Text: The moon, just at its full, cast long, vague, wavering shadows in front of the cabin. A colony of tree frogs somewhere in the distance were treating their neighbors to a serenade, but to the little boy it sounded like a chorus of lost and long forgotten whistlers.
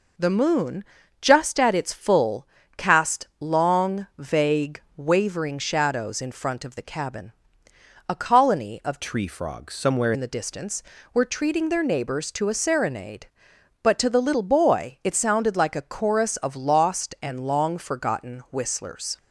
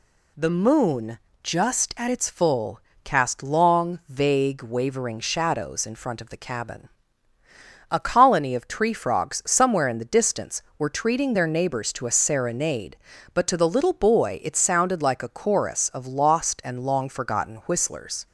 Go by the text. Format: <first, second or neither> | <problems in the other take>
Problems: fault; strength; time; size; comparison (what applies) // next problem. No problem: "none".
second | changes voice from "tree" to "somewhere"; from 9.0 to 10.1 s; 1.1 s long